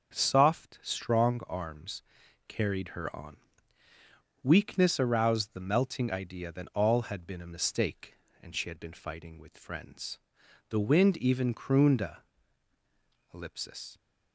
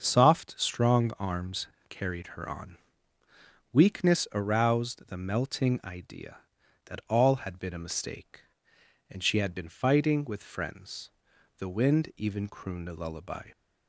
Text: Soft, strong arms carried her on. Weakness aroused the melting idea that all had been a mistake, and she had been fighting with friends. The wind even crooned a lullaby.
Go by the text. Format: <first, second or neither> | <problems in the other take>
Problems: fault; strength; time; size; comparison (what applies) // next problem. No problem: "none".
second | starts louder than the rest; until 1.1 s; 6.5 dB; also in the second // pauses between "arms" and "carried"; at 2.0 s; 0.44 s long; slight in the second // says "ellipsis" for "lullaby"; at 13.3 s